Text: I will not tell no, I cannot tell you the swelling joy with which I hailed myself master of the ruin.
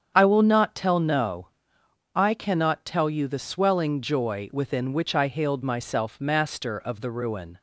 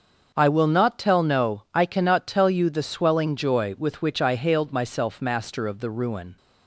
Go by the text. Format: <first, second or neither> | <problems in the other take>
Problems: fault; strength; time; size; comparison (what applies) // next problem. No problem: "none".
second | starts louder than the rest; strong; until 1.1 s; 8 dB; also in the second // says "within" for "with"; at 4.5 s